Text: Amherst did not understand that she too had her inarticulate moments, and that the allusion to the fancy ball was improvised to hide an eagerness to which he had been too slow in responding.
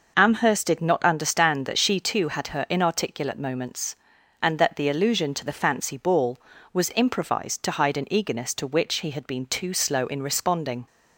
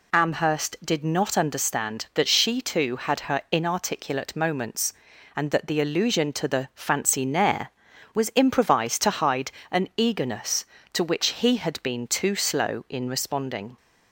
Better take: first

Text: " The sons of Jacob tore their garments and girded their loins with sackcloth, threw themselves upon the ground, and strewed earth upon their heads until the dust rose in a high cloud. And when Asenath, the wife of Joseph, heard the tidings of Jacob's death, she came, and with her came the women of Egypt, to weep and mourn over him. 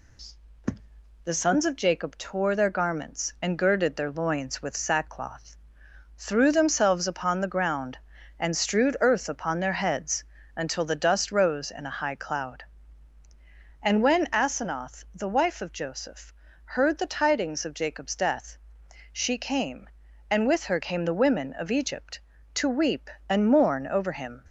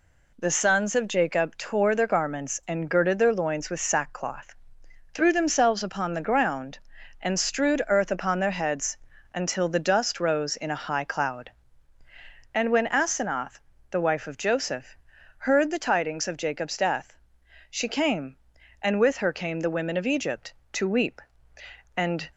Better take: first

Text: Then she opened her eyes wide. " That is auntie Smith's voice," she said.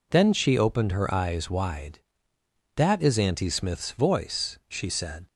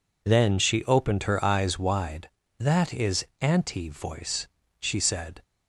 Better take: first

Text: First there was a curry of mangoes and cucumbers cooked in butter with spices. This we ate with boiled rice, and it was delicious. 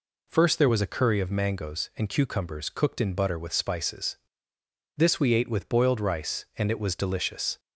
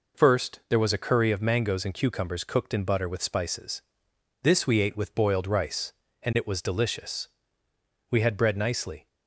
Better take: first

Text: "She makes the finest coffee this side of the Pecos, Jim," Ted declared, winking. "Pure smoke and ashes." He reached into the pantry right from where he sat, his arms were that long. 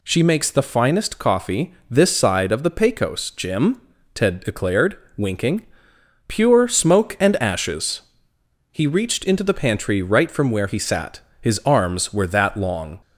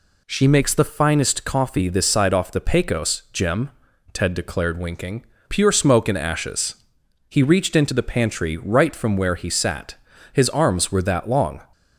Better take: first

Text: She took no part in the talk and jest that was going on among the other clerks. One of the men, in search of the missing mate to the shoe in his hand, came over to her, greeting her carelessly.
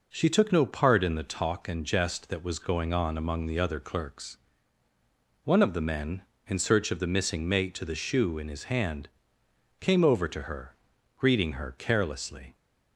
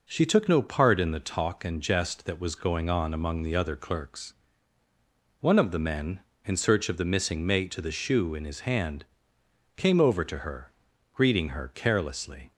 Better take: neither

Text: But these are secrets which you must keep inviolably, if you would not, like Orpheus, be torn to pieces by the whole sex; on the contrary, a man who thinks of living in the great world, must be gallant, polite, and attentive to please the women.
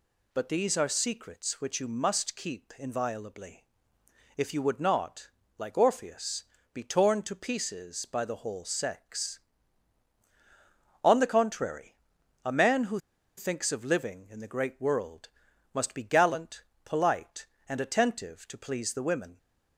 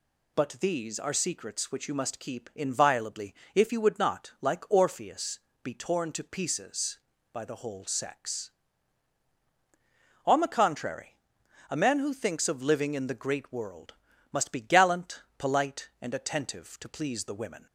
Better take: second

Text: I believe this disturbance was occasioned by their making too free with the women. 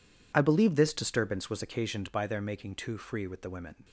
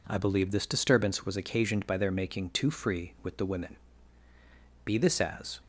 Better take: first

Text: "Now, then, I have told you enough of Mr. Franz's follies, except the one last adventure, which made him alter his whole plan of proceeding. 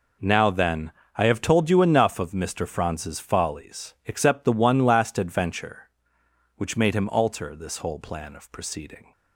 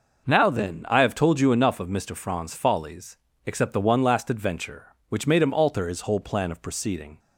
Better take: second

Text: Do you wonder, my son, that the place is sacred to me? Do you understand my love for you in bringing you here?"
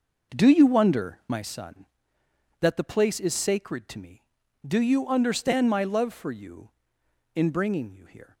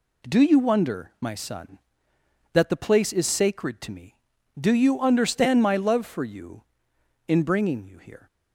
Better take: second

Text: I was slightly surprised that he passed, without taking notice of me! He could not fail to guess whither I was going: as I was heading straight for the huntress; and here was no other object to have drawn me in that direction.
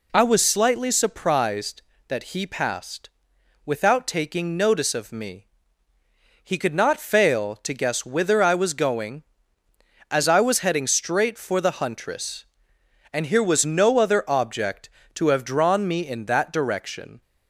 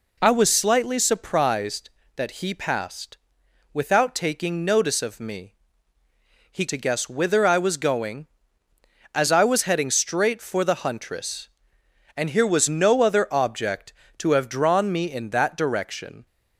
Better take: first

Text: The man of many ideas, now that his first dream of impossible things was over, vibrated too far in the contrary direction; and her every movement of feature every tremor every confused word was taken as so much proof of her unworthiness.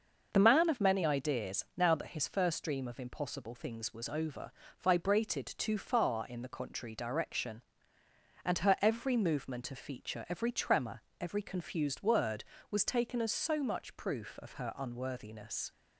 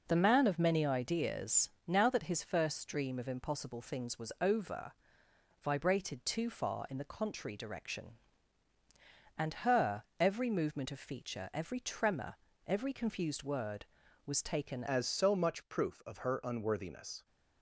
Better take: first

